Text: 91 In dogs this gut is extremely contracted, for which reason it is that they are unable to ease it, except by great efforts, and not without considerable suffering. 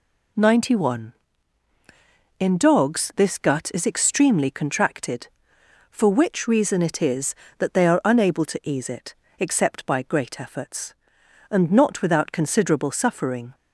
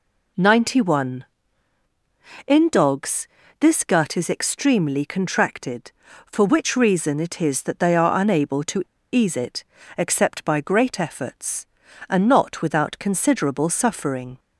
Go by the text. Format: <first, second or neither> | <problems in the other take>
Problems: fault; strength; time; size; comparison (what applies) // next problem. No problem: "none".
first | pauses between "dogs" and "this"; slight; at 3.2 s; 0.32 s long // pauses between "to" and "ease"; slight; at 8.8 s; 0.30 s long